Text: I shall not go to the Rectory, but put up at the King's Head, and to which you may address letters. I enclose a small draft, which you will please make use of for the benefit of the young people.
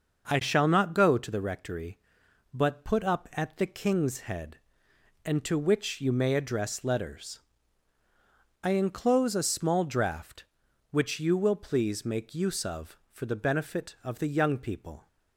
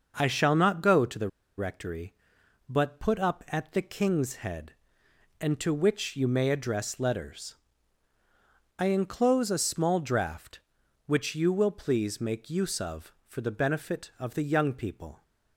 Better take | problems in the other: first | starts louder than the rest; noticeable; until 1.1 s; 6 dB; noticeable in the first // pauses between "the" and "Rectory"; slight; at 1.2 s; 0.30 s long

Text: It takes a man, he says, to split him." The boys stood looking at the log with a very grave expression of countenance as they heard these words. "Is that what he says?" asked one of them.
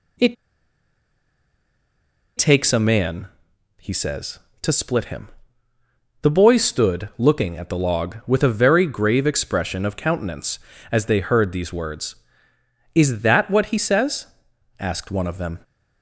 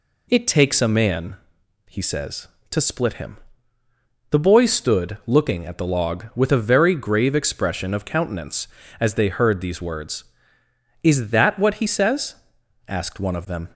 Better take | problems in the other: second | pauses between "It" and "takes"; strong; at 0.3 s; 2.0 s long

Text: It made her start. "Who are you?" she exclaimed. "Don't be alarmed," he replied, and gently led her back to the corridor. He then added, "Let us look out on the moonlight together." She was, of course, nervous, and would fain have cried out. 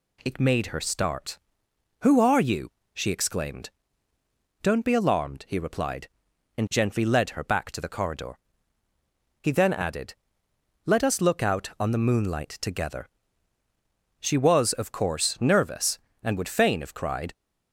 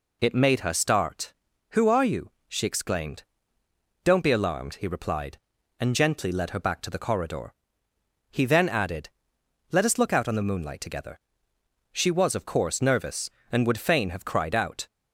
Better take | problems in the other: second | stops before "out"; at 17.3 s

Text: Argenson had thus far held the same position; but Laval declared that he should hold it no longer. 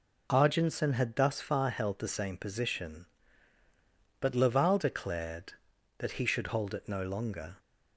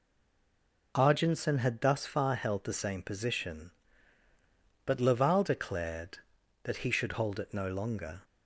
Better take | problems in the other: first | stays silent before the first word; slight; until 0.9 s; 0.9 s long

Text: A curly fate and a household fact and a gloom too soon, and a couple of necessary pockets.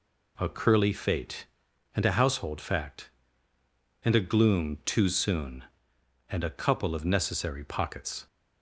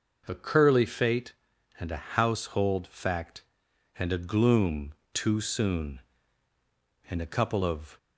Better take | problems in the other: first | pauses between "gloom" and "too"; slight; at 4.9 s; 0.20 s long // stops before "necessary pockets"; at 7.9 s

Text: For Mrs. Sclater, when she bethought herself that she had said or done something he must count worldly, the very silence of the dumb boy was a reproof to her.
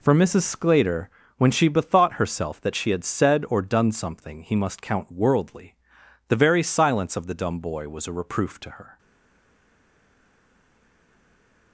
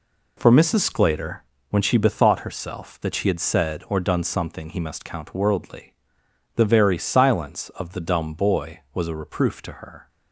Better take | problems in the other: second | stays silent after the last word; strong; from 8.9 s on; 2.8 s long

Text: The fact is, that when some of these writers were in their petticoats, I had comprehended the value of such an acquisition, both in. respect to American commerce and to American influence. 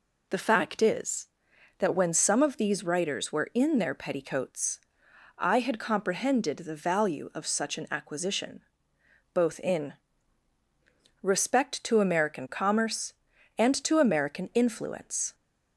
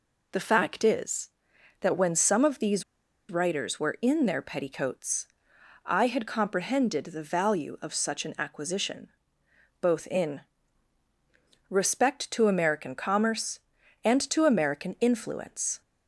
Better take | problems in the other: first | pauses between "these" and "writers"; noticeable; at 2.8 s; 0.47 s long

